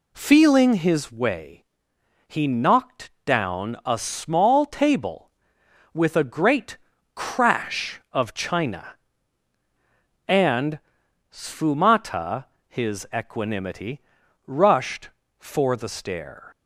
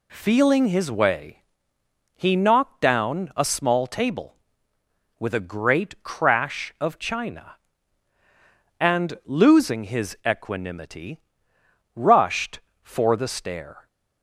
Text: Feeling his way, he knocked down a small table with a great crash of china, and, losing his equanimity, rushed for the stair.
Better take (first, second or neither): second